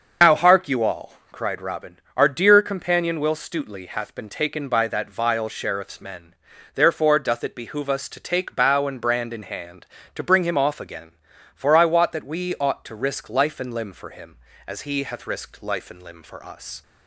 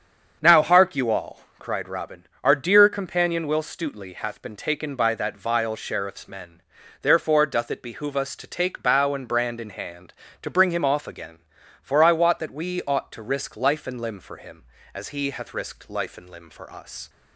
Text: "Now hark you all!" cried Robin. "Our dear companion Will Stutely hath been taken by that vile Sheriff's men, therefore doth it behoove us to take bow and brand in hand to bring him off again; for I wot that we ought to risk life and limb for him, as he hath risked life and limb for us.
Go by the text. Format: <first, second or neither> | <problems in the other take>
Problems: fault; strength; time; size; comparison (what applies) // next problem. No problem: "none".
second | loses the start of "Now"; at 0.2 s; 70 ms // starts louder than the rest; until 1.3 s; 6.5 dB; also in the second